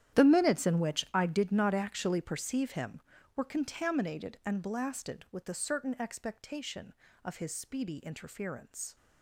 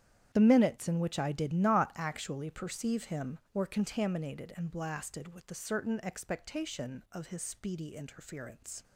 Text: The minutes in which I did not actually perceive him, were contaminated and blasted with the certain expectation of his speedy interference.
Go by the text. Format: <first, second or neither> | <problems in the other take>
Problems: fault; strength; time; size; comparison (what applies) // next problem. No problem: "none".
second | gets quieter; strong; throughout; 16 dB // starts louder than the rest; strong; until 1.2 s; 11 dB; strong in the second